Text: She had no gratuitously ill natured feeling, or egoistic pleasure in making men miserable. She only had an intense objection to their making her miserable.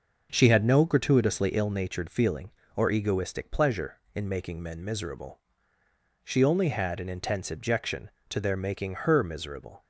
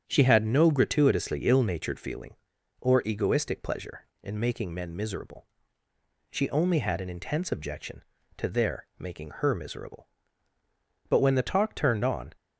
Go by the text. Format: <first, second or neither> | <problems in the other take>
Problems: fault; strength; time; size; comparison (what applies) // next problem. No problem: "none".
first | starts louder than the rest; strong; until 1.0 s; 8.5 dB; also in the first // goes on to say "But when the talk turned on"; noticeable; from 11.0 s on; 1.2 s long